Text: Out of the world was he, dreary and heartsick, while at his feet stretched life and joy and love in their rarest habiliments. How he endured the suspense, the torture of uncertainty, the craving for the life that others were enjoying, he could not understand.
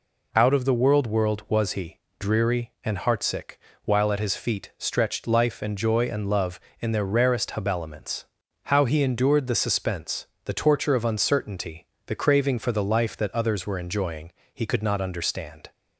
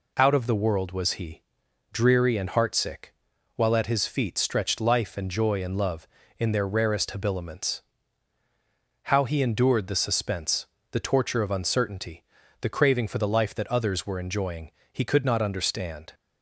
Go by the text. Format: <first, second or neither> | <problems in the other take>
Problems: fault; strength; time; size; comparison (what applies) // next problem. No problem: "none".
second | says "world" twice; at 1.0 s